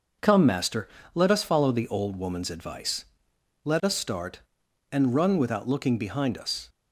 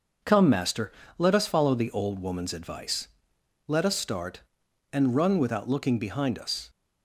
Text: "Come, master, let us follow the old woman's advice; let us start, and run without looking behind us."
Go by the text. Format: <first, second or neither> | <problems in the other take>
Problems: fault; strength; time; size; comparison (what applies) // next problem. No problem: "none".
neither | none